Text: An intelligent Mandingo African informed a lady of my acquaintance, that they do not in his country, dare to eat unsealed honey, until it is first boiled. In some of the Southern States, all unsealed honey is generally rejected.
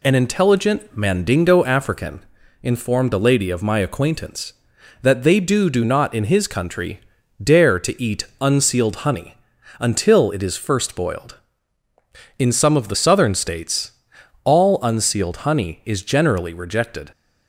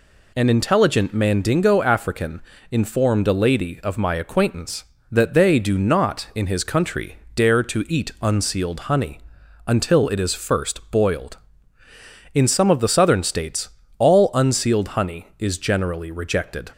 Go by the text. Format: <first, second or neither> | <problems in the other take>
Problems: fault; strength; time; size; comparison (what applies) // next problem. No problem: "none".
second | pauses between "African" and "informed"; at 2.2 s; 0.40 s long; slight in the second // says "do" twice; at 5.6 s // pauses between "eat" and "unsealed"; slight; at 8.2 s; 0.16 s long